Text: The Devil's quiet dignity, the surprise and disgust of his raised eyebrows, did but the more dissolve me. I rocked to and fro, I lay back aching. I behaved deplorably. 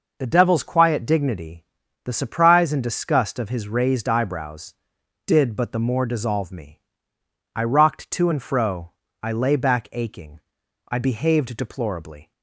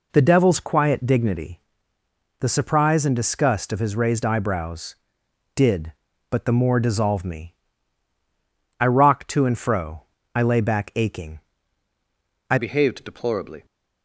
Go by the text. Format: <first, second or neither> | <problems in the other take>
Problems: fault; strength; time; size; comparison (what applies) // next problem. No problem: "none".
first | changes voice at "behaved"; from 12.5 s on; 1.1 s long